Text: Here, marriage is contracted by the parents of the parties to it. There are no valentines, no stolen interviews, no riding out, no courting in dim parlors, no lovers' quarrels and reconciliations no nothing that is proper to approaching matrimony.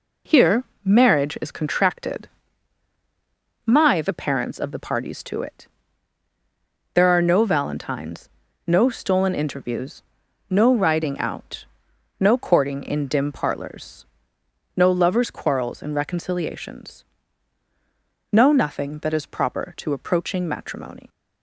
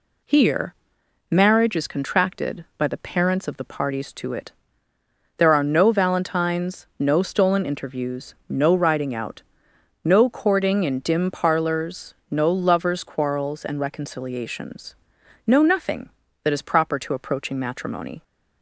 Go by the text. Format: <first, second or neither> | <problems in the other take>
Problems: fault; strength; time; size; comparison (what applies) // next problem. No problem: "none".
second | says "my" for "by"; at 3.6 s // pauses between "reconciliations" and "no"; strong; at 17.0 s; 1.2 s long; noticeable in the second